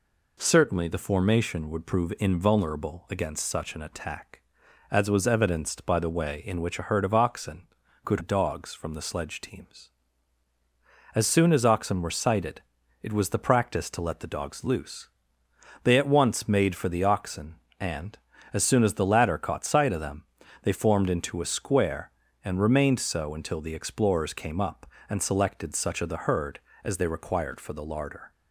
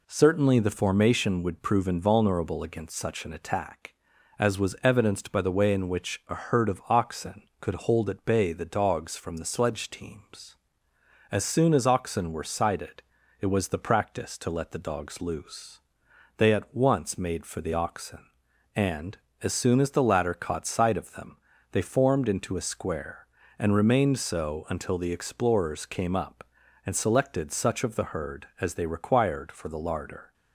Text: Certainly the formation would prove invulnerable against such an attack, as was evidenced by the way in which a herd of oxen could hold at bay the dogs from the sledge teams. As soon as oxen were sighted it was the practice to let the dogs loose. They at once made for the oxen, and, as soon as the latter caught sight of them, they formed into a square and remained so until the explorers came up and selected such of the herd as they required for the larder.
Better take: second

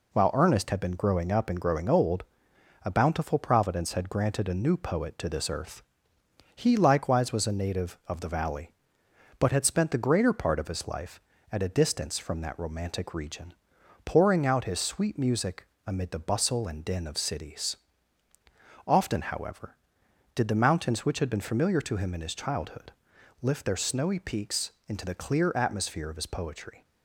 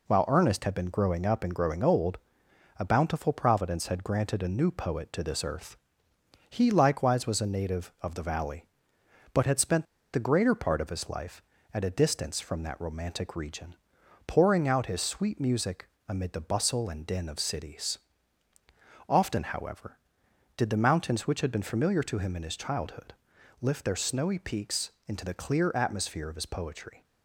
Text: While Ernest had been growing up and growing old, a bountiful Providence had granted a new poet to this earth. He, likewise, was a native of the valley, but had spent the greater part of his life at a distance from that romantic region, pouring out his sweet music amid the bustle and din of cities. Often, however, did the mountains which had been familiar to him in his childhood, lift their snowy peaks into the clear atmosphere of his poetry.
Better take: first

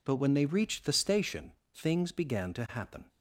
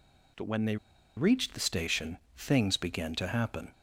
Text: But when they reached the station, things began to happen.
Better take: first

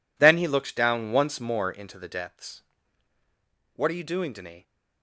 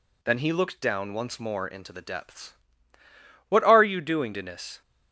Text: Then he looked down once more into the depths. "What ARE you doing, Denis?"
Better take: neither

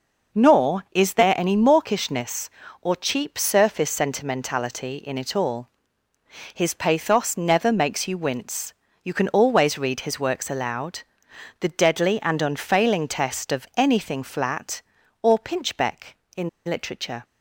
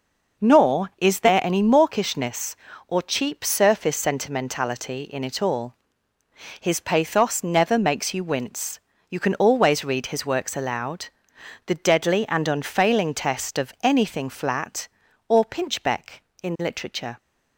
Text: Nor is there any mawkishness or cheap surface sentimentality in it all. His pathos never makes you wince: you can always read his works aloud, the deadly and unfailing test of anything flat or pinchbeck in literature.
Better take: second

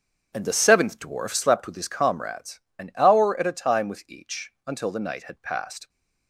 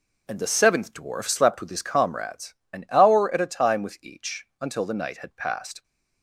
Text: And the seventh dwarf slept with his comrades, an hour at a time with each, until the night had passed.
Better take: second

